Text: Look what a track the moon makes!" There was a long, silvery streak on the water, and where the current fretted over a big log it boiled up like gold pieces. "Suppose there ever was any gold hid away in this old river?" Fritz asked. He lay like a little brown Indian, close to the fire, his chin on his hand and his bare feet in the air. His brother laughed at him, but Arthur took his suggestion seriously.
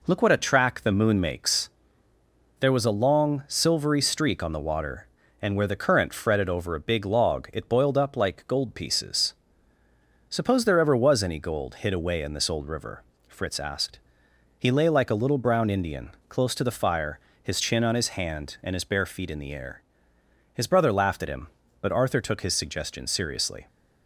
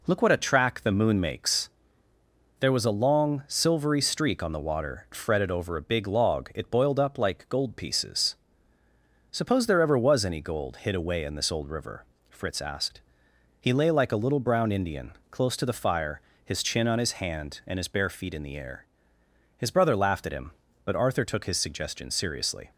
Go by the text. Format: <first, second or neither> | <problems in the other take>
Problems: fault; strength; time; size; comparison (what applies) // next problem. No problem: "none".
first | skips "and where the current"; at 5.1 s